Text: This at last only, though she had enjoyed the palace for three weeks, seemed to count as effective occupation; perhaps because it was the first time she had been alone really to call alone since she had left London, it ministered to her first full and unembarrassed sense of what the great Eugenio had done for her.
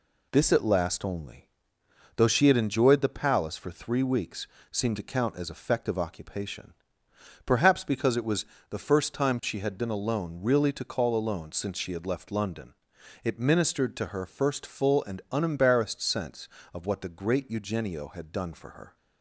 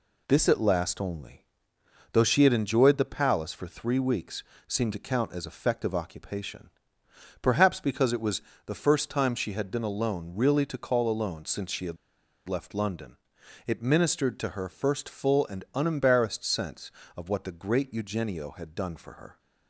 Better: first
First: pauses between "was" and "the"; slight; at 8.4 s; 0.24 s long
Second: pauses between "was" and "the"; slight; at 8.4 s; 0.24 s long // pauses between "had" and "left"; noticeable; at 11.9 s; 0.51 s long

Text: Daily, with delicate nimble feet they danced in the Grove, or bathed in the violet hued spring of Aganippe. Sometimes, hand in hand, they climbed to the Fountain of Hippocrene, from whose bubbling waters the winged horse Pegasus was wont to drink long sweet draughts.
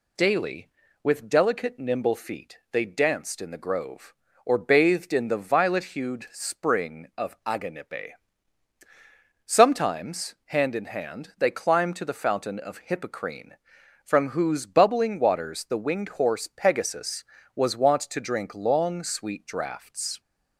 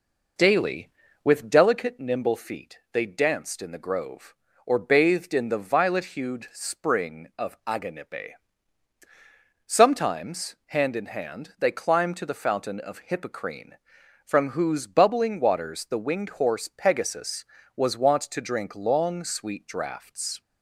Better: first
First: pauses between "feet" and "they"; slight; at 2.5 s; 0.16 s long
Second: starts louder than the rest; noticeable; until 1.9 s; 4.5 dB // pauses between "feet" and "they"; slight; at 2.7 s; 0.16 s long

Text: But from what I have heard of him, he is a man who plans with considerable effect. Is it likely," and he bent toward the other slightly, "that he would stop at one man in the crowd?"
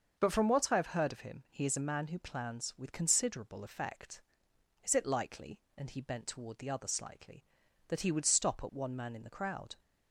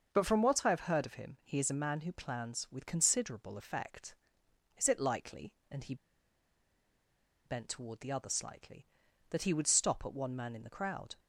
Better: first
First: starts louder than the rest; until 1.1 s; 6.5 dB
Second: starts louder than the rest; until 1.1 s; 6.5 dB // pauses between "he" and "bent"; strong; at 5.9 s; 1.5 s long

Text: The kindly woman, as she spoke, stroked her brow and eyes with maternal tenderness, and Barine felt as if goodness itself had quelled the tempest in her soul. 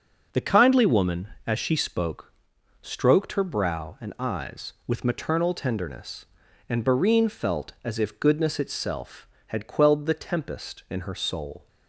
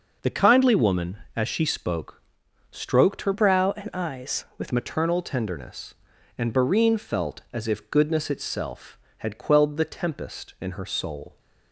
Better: first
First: none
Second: changes voice from "brow" to "with"; from 3.3 to 4.7 s; 1.4 s long

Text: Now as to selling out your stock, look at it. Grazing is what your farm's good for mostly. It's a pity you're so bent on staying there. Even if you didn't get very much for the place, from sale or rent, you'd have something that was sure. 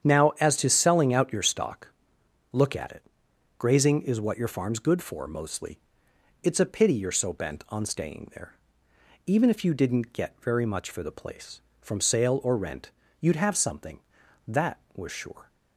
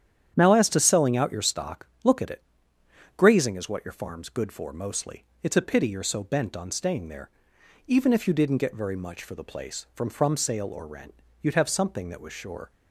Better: first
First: starts louder than the rest; strong; until 1.1 s; 9 dB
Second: starts louder than the rest; strong; until 1.3 s; 9.5 dB // says "from" twice; at 10.0 s

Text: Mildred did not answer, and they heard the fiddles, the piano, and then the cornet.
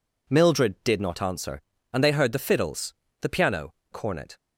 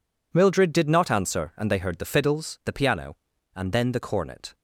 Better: second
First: skips "and then the"; at 3.8 s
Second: none

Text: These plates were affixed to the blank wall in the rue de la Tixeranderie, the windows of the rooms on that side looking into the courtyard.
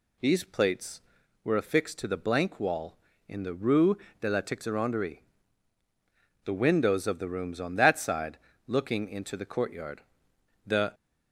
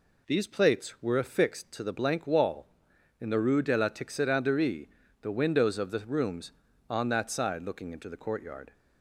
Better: second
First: pauses between "rue" and "de"; slight; at 3.9 s; 0.24 s long // pauses between "side" and "looking"; slight; at 8.3 s; 0.28 s long // goes on to say "The"; slight; from 10.6 s on; 0.28 s long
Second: none

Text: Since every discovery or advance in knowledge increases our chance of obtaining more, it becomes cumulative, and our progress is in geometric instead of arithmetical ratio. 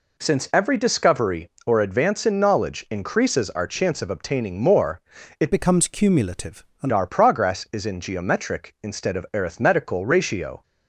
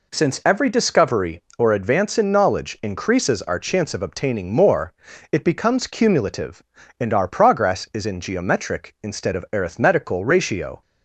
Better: second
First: changes voice from "becomes" to "and"; from 5.5 to 6.9 s; 1.4 s long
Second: none

